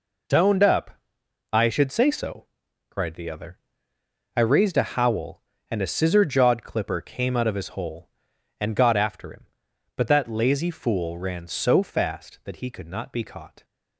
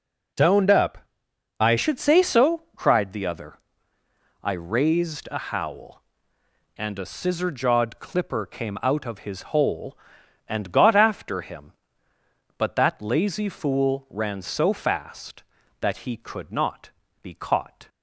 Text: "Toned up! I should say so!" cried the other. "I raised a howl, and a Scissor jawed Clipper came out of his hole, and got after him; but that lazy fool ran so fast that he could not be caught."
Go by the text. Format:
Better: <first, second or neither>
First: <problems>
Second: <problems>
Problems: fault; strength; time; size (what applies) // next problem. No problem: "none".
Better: first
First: none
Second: changes voice at "should"; from 1.7 s on; 16.1 s long // pauses between "not" and "be"; slight; at 16.9 s; 0.32 s long